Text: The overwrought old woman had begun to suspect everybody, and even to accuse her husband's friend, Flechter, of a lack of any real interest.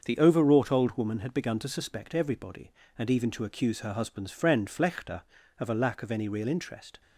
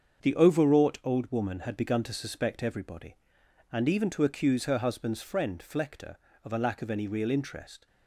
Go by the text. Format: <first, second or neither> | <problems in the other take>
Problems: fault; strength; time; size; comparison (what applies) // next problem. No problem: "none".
neither | starts louder than the rest; the same in both